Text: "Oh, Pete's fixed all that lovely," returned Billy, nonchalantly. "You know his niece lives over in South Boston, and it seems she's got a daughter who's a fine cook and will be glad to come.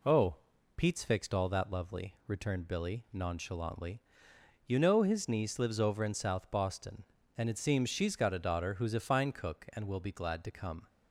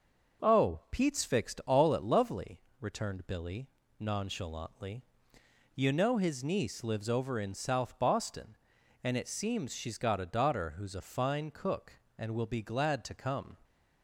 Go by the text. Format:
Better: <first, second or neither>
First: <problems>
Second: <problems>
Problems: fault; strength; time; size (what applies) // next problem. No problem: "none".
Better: first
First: none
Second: says "at" for "that"; at 1.9 s